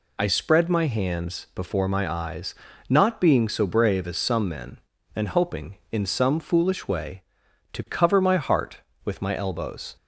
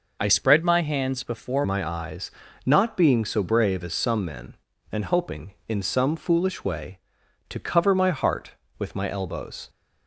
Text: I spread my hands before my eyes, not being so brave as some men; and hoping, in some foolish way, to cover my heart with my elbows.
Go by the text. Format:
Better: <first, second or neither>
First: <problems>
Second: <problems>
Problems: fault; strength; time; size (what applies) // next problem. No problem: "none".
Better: first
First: none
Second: changes voice from "spread" to "before"; from 0.2 to 1.6 s; 1.4 s long